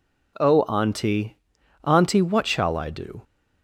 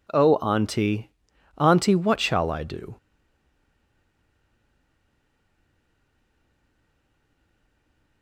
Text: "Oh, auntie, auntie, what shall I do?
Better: first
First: none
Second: stays silent after the last word; strong; from 2.9 s on; 5.3 s long

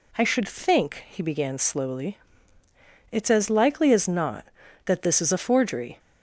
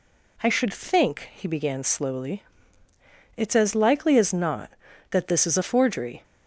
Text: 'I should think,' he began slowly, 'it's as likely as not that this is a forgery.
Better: neither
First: none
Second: none

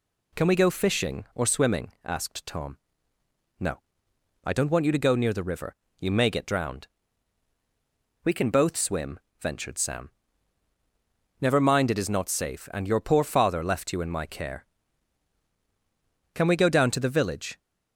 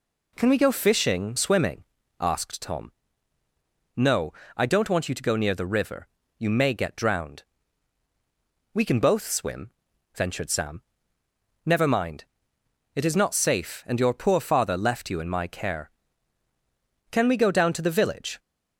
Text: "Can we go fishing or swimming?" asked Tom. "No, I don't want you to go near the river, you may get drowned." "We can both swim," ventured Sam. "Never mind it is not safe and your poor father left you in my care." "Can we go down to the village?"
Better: first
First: none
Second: skips "or"; at 1.3 s // pauses between "mind" and "it"; noticeable; at 12.2 s; 0.70 s long

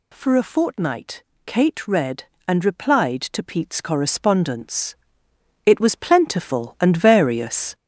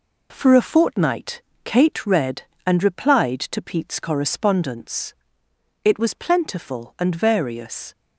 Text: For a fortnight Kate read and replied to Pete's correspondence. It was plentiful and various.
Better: second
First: gets louder; noticeable; throughout; 6 dB // pauses between "fortnight" and "Kate"; slight; at 1.2 s; 0.22 s long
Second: pauses between "fortnight" and "Kate"; slight; at 1.4 s; 0.22 s long

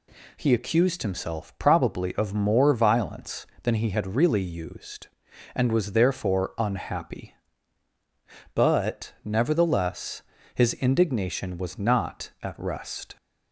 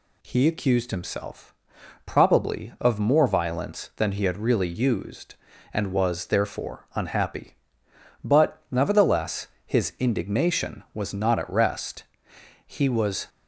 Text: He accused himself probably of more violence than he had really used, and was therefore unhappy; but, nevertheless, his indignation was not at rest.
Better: first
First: none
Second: pauses between "himself" and "probably"; noticeable; at 1.5 s; 0.50 s long // goes on to say "He was"; noticeable; from 12.6 s on; 0.62 s long

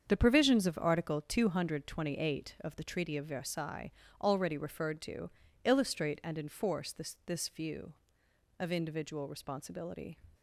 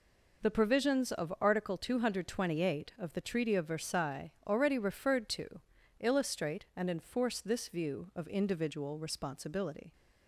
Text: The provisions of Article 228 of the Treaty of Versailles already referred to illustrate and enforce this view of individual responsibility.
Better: second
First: starts louder than the rest; strong; until 1.0 s; 7 dB // pauses between "Versailles" and "already"; slight; at 3.9 s; 0.30 s long // pauses between "to" and "illustrate"; slight; at 5.2 s; 0.36 s long // says "this" twice; at 7.2 s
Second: pauses between "Versailles" and "already"; slight; at 4.2 s; 0.16 s long // pauses between "to" and "illustrate"; at 5.5 s; 0.40 s long

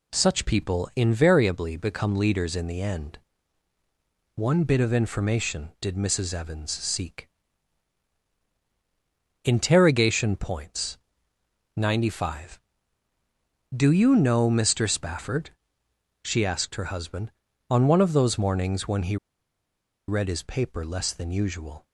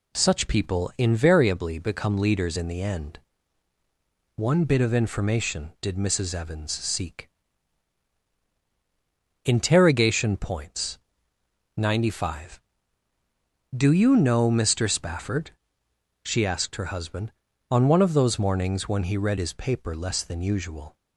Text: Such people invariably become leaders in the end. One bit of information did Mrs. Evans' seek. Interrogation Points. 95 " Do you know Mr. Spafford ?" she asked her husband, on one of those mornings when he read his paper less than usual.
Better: second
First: pauses between "he" and "read"; noticeable; at 19.1 s; 0.92 s long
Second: none

